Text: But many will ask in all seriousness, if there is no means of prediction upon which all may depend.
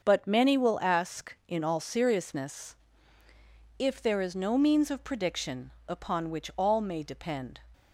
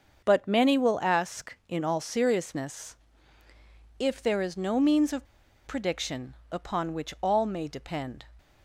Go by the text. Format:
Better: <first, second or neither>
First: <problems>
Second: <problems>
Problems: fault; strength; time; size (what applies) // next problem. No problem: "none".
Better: first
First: starts louder than the rest; until 1.0 s; 6.5 dB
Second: starts louder than the rest; until 1.2 s; 6.5 dB // pauses between "of" and "prediction"; at 5.2 s; 0.41 s long